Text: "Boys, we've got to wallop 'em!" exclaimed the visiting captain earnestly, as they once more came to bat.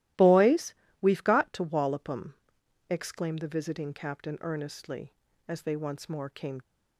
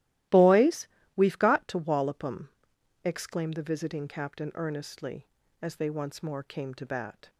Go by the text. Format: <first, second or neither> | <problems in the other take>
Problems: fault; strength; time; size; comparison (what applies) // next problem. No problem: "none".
second | starts louder than the rest; strong; until 1.4 s; 15 dB; strong in the second // stops before "to bat"; at 6.6 s